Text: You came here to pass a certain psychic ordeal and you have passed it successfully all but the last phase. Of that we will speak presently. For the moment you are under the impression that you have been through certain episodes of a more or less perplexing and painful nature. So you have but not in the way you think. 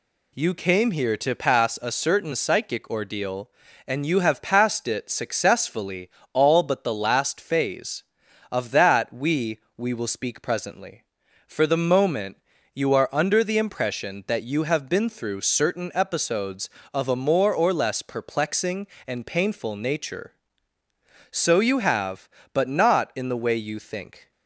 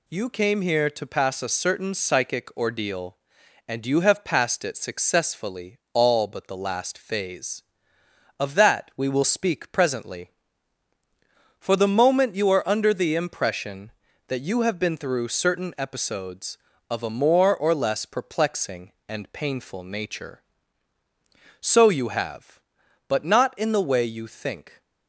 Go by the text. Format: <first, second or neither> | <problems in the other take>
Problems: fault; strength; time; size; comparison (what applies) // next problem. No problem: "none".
second | pauses between "successfully" and "all"; slight; at 6.0 s; 0.24 s long // says "we" twice; at 9.7 s // pauses between "moment" and "you"; slight; at 12.3 s; 0.36 s long